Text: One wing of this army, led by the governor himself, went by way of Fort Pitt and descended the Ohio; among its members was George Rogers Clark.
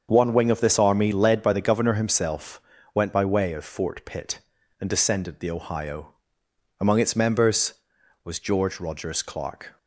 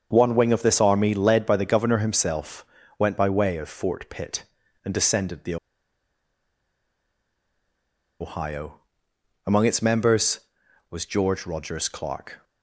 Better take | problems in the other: first | starts louder than the rest; until 1.1 s; 7 dB; also in the first // pauses between "the" and "Ohio"; strong; at 5.5 s; 2.6 s long

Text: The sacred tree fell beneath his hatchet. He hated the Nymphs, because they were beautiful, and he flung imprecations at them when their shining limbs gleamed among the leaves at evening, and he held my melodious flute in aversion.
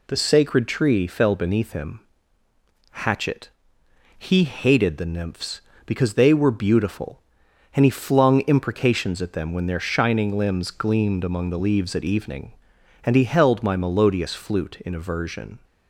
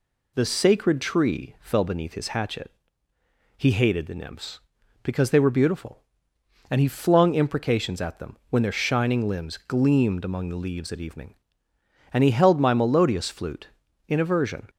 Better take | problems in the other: second | says "him" for "his"; at 1.7 s

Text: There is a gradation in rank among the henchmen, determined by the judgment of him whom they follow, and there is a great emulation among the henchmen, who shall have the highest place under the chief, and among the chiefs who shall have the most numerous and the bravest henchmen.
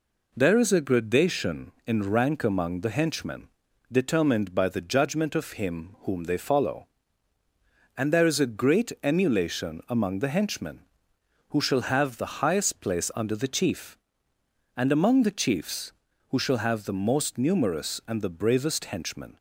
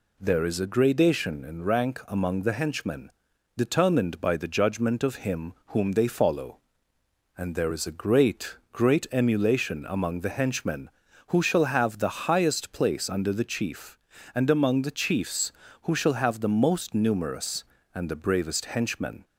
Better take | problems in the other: first | says "great" twice; at 8.7 s

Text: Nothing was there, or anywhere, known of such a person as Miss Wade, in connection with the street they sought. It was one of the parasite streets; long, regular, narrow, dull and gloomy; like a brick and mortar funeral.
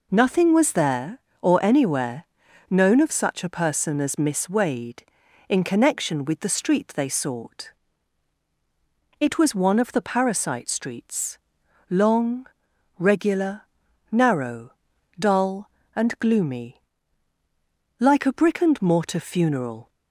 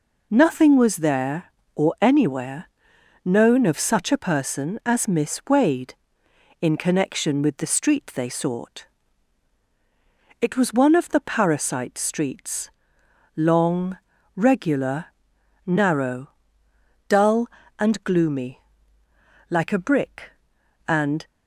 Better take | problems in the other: first | stops before "mortar funeral"; at 21.2 s

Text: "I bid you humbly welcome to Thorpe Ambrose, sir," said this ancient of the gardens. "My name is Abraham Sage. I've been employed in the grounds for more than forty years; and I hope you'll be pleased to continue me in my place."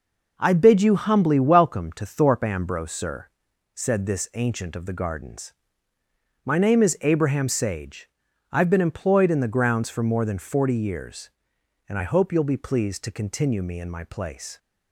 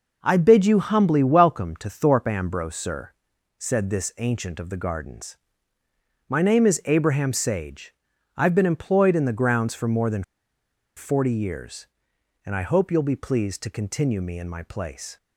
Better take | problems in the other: first | pauses between "than" and "forty"; noticeable; at 10.2 s; 0.73 s long

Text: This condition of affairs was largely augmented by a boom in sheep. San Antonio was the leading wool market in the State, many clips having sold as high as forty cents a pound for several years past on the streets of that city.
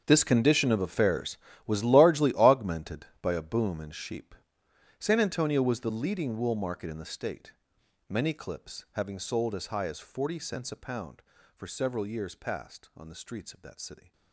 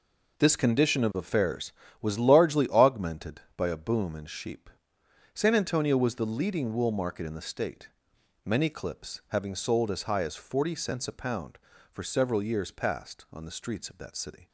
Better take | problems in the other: second | gets quieter; strong; throughout; 17 dB

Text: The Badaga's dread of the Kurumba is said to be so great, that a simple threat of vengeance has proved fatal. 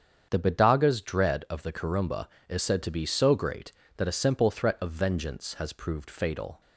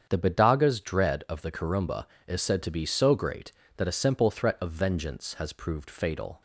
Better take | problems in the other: neither | starts louder than the rest; strong; the same in both

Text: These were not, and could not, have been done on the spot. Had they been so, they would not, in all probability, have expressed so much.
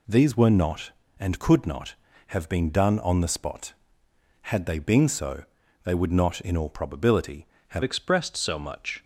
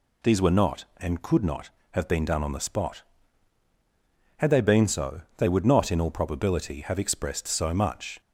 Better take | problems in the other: second | changes voice at "expressed"; from 7.8 s on; 1.2 s long

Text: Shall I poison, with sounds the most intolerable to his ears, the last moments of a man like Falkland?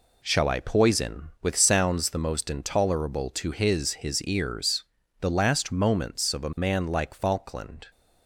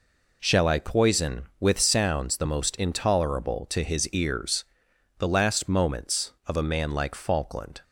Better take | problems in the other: second | says "his" twice; at 3.9 s

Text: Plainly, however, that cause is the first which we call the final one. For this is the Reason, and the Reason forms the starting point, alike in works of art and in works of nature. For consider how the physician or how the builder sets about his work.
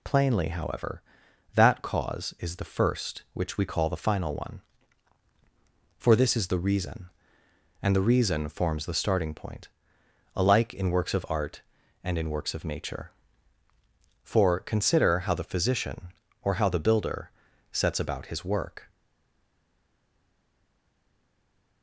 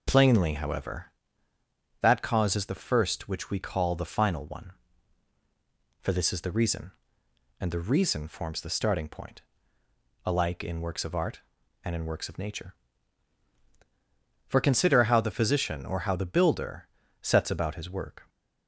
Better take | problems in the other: second | pauses between "builder" and "sets"; at 17.3 s; 0.42 s long; slight in the second // stays silent after the last word; strong; from 18.9 s on; 2.9 s long

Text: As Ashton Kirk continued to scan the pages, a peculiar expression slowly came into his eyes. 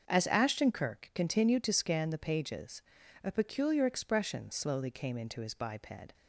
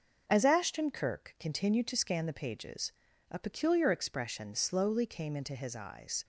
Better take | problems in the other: second | starts louder than the rest; until 1.0 s; 6.5 dB // says "biped" for "eyes"; at 5.5 s

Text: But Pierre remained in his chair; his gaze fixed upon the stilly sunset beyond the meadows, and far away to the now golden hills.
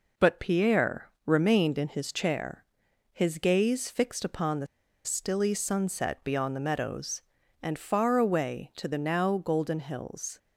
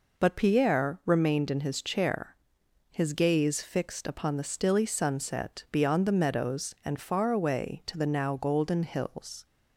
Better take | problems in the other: second | pauses between "Pierre" and "remained"; slight; at 1.0 s; 0.16 s long // pauses between "the" and "stilly"; at 4.6 s; 0.39 s long

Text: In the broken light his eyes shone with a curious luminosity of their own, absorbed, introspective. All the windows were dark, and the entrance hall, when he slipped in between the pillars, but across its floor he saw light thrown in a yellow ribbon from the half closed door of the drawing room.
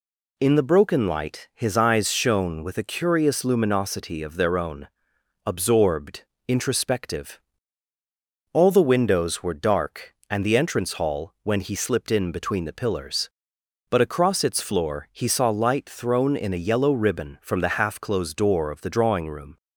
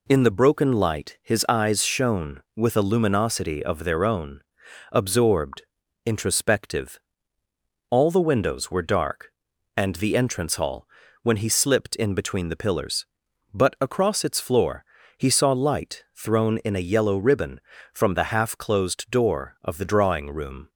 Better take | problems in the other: first | skips "curious"; at 2.8 s // pauses between "floor" and "he"; slight; at 14.8 s; 0.32 s long

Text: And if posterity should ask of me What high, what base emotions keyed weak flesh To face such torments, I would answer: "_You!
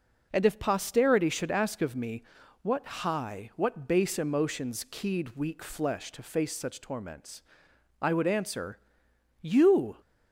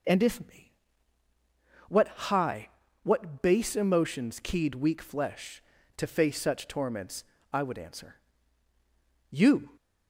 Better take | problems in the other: first | skips "posterity should ask of"; at 0.4 s // pauses between "me" and "What"; at 0.7 s; 1.1 s long; also in the first

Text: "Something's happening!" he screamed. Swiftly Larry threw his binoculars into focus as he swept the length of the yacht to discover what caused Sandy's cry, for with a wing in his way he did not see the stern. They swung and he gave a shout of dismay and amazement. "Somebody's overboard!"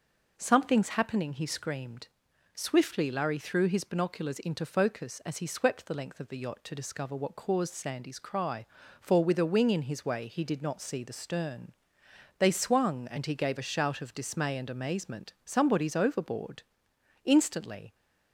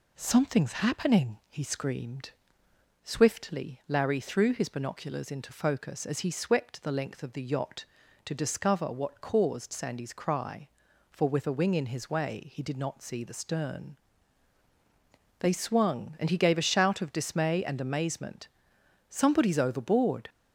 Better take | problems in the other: second | goes on to say "Instantly"; noticeable; from 17.2 s on; 0.70 s long

